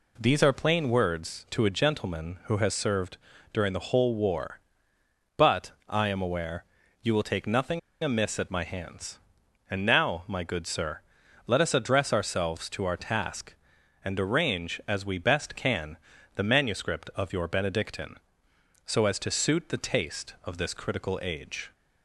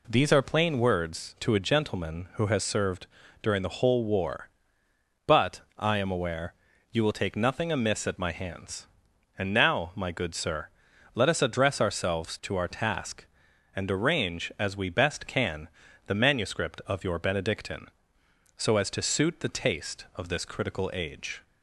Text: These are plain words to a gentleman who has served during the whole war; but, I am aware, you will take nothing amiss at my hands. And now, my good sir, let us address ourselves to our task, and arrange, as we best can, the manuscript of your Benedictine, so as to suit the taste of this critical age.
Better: second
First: pauses between "served" and "during"; slight; at 3.1 s; 0.34 s long // pauses between "nothing" and "amiss"; slight; at 7.7 s; 0.24 s long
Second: pauses between "served" and "during"; slight; at 3.0 s; 0.34 s long

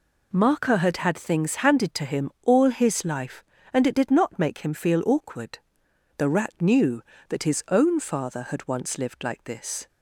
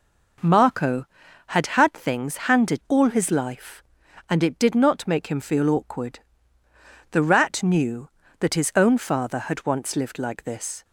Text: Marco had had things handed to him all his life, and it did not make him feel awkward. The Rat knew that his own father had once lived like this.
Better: first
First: none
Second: skips "to him"; at 2.8 s

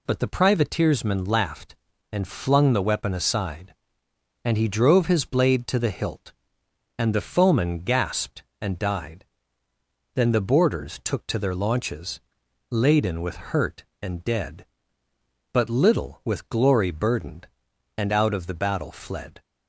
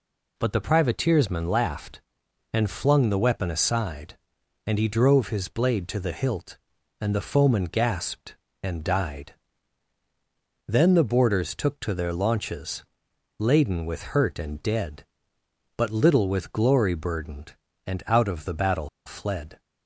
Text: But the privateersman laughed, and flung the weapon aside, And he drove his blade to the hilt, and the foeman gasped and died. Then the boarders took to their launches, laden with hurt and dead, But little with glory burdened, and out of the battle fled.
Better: first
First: none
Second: pauses between "battle" and "fled"; slight; at 18.8 s; 0.17 s long

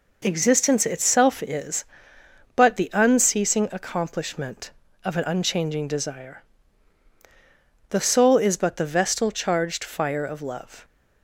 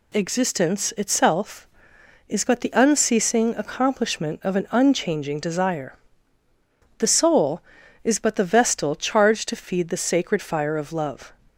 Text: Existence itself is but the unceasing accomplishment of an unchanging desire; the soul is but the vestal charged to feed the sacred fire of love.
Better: second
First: skips "to feed the sacred"; at 9.8 s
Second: none

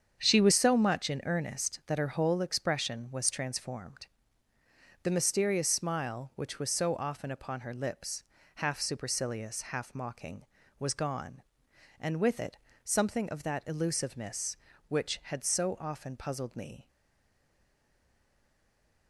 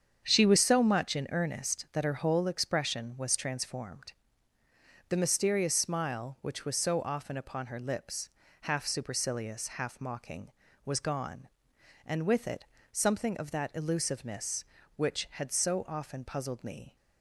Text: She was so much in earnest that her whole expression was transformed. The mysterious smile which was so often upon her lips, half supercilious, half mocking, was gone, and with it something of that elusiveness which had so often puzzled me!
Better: second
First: starts louder than the rest; strong; until 1.2 s; 7.5 dB // pauses between "it" and "something"; slight; at 12.5 s; 0.30 s long // stays silent after the last word; from 16.8 s on; 2.2 s long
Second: starts louder than the rest; strong; until 1.2 s; 7.5 dB // pauses between "it" and "something"; slight; at 12.6 s; 0.30 s long

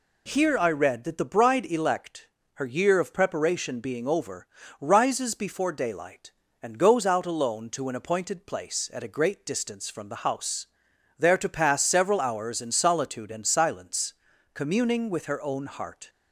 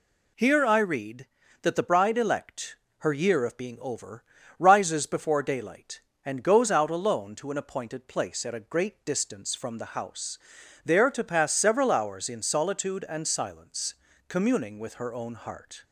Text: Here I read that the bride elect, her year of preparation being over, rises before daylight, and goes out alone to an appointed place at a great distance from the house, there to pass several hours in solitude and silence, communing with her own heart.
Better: first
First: none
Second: skips "preparation"; at 3.5 s

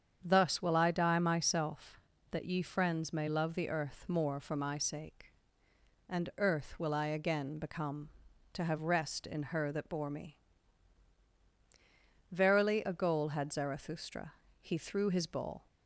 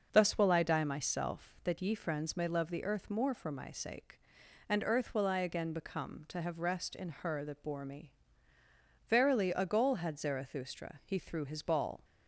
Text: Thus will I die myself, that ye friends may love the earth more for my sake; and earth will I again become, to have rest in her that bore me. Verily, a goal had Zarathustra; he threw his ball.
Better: neither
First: starts louder than the rest; strong; until 1.2 s; 7.5 dB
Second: starts louder than the rest; until 1.1 s; 6 dB

